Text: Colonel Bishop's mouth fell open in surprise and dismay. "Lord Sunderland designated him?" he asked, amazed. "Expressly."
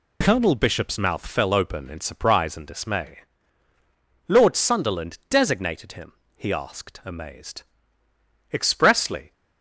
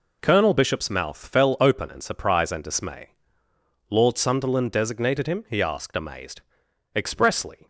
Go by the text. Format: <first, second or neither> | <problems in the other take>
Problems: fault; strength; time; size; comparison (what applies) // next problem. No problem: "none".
neither | none